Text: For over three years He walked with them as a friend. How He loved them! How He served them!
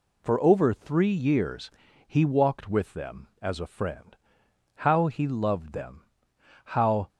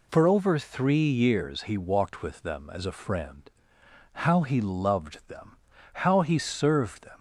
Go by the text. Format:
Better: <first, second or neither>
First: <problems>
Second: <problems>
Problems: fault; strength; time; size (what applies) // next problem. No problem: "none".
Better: second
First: pauses between "years" and "He"; at 1.6 s; 0.38 s long // stops before "He served them"; at 7.0 s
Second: none